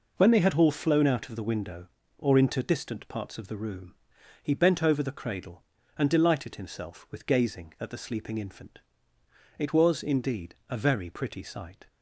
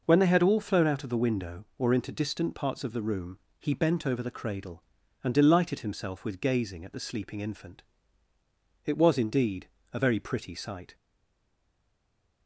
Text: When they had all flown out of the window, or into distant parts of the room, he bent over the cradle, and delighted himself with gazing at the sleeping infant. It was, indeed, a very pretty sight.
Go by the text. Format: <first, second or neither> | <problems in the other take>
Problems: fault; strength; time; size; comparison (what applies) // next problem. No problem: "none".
first | stays silent after the last word; noticeable; from 10.9 s on; 1.5 s long